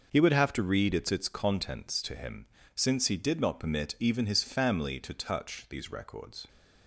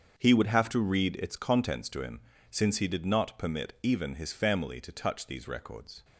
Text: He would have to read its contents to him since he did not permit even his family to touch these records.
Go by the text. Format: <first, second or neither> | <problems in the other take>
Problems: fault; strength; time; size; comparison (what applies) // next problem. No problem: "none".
second | starts louder than the rest; noticeable; until 1.1 s; 6 dB; also in the second // says "its" twice; at 1.1 s // pauses between "him" and "since"; slight; at 2.4 s; 0.28 s long; slight in the second